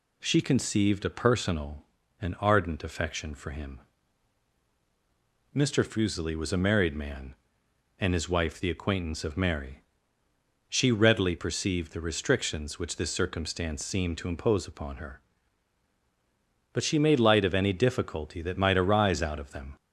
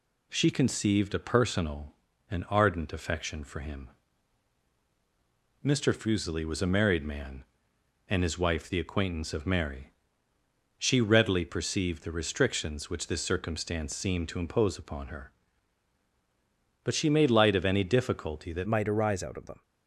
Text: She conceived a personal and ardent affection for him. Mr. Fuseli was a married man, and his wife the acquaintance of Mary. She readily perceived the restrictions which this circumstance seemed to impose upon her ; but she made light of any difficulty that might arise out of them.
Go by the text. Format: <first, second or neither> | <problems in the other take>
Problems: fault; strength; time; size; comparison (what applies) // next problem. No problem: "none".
first | changes voice at "might"; from 18.6 s on; 1.0 s long